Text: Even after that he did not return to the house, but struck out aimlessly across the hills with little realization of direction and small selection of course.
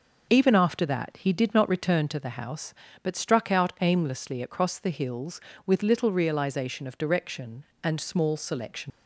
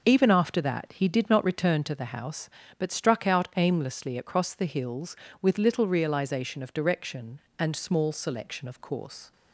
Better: second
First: stops before "of course"; at 8.9 s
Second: none

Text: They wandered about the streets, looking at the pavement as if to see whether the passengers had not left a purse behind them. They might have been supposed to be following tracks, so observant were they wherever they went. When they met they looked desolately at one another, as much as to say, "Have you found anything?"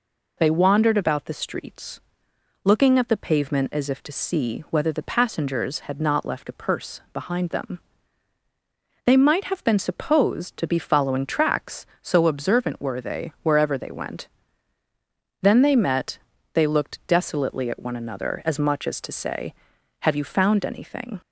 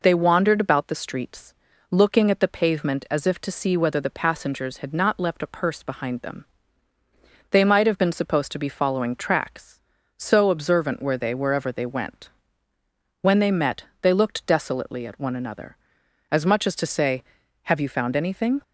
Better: second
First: says "Then" for "When"; at 15.4 s // pauses between "met" and "they"; slight; at 16.1 s; 0.36 s long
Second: pauses between "met" and "they"; slight; at 13.8 s; 0.16 s long

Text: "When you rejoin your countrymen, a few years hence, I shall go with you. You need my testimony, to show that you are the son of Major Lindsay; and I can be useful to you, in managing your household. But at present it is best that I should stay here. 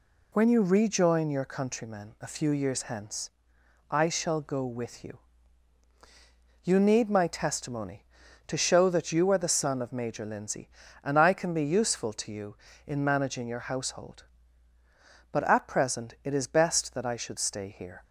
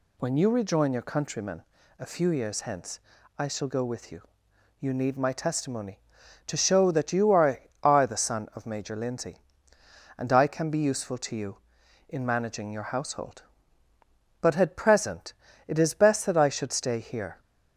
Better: first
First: none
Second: says "are" twice; at 7.8 s // pauses between "present" and "it"; slight; at 15.3 s; 0.34 s long

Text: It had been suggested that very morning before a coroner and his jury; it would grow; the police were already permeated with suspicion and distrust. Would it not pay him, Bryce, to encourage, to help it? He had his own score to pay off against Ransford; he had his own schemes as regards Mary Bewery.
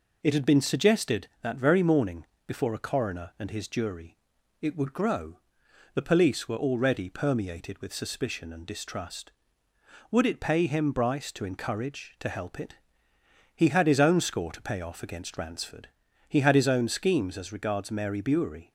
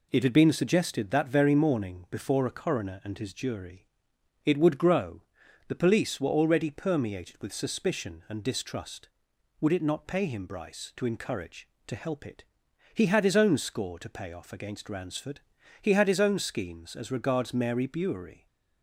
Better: second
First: pauses between "morning" and "before"; slight; at 2.2 s; 0.22 s long // skips "not"; at 10.3 s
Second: none

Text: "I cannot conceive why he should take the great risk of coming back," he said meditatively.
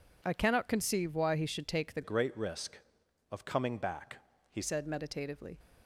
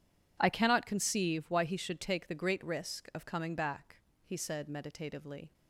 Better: second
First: changes voice from "great" to "he"; from 2.0 to 4.6 s; 2.6 s long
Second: none

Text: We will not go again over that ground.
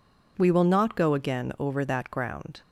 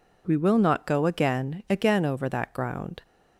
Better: first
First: none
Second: says "again" twice; at 1.6 s

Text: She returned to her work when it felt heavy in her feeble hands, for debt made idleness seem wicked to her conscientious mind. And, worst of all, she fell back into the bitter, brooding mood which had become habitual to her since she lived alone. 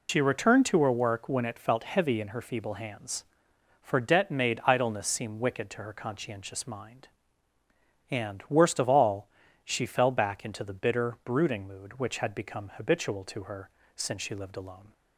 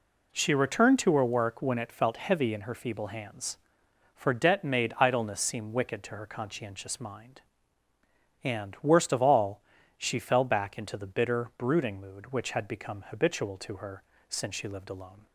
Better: second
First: loses the start of "She"; at 0.0 s; 110 ms // pauses between "her" and "since"; slight; at 13.6 s; 0.28 s long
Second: pauses between "her" and "since"; slight; at 14.0 s; 0.28 s long

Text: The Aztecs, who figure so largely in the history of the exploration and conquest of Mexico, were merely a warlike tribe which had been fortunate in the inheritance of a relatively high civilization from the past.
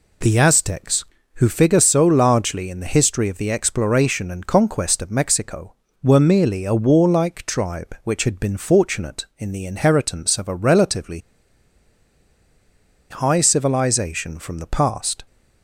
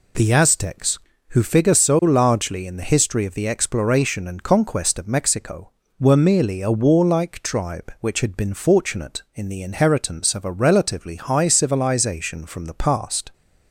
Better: second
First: pauses between "relatively" and "high"; strong; at 11.1 s; 1.9 s long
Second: none

